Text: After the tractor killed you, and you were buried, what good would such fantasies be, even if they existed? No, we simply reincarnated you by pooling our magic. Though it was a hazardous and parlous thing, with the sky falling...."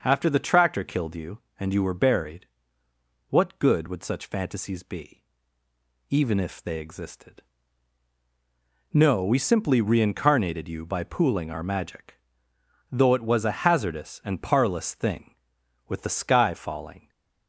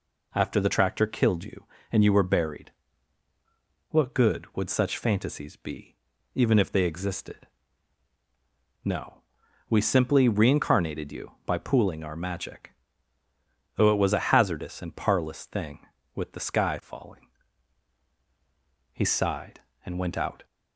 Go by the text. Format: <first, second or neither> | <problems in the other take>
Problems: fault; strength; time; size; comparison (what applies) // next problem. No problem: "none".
first | goes on to say "He sighed and went out"; from 18.9 s on; 1.5 s long